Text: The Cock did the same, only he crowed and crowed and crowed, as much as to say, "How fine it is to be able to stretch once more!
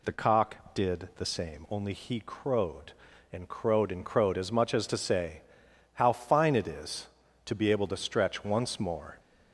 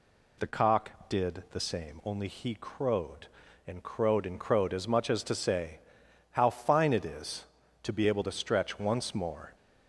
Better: neither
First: none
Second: none

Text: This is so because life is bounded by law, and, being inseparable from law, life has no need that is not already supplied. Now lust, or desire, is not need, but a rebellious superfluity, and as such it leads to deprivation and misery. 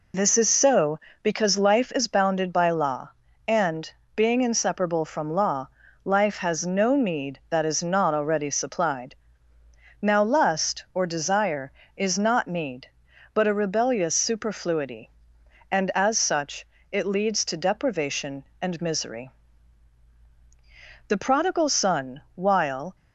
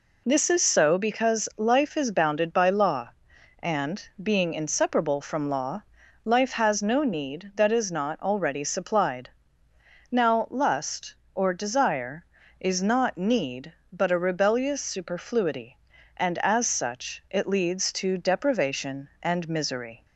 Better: second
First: pauses between "such" and "it"; slight; at 16.6 s; 0.28 s long // goes on to say "The prodigal son while"; strong; from 21.0 s on; 1.8 s long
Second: none

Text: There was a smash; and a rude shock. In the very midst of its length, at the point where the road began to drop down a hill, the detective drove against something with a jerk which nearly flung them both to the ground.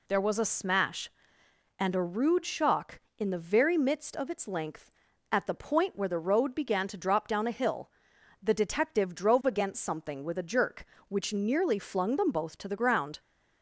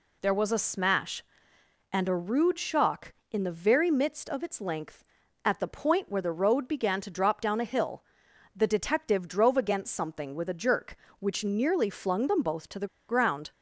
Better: first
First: none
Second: pauses between "the" and "ground"; slight; at 12.8 s; 0.22 s long

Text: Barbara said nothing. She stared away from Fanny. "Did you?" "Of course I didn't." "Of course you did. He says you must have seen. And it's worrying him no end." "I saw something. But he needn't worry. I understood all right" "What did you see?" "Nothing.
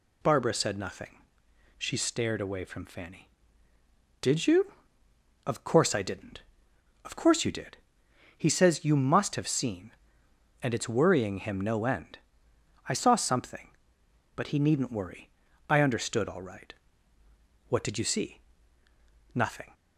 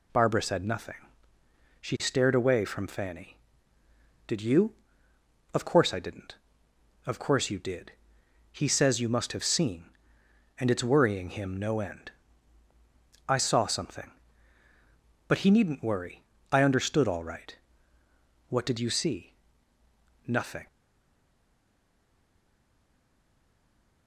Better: first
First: pauses between "right" and "What"; noticeable; at 16.7 s; 0.96 s long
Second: pauses between "right" and "What"; noticeable; at 17.5 s; 0.92 s long // stays silent after the last word; strong; from 20.6 s on; 3.4 s long

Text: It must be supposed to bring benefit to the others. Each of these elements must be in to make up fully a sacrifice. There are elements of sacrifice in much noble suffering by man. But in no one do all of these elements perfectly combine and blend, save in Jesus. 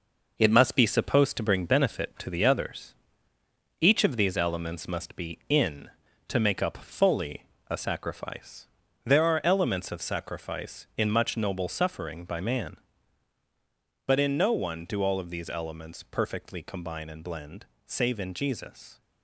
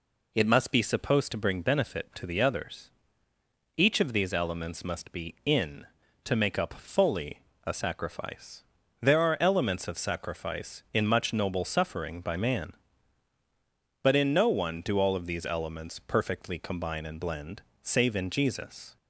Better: second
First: gets quieter; throughout; 7 dB // pauses between "fully" and "a"; slight; at 7.4 s; 0.24 s long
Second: pauses between "fully" and "a"; slight; at 7.4 s; 0.24 s long

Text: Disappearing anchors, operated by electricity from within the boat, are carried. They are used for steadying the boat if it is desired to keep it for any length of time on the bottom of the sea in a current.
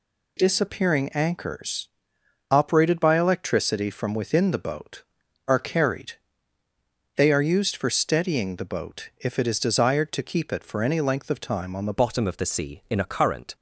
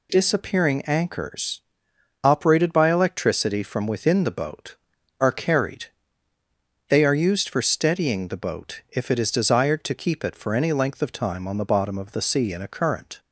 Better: second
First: changes voice at "bottom"; from 11.9 s on; 1.6 s long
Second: none

